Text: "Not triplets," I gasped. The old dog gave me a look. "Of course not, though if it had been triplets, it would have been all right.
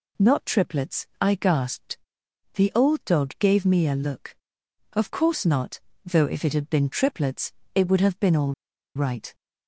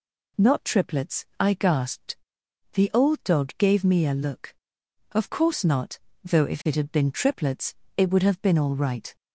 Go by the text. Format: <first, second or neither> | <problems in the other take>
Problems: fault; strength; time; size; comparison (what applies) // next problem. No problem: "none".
second | pauses between "all" and "right"; at 8.5 s; 0.42 s long